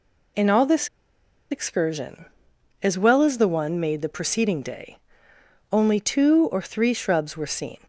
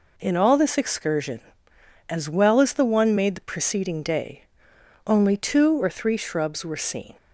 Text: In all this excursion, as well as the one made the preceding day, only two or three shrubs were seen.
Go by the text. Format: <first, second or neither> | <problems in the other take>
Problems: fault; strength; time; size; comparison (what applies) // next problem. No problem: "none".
second | pauses between "this" and "excursion"; noticeable; at 0.8 s; 0.62 s long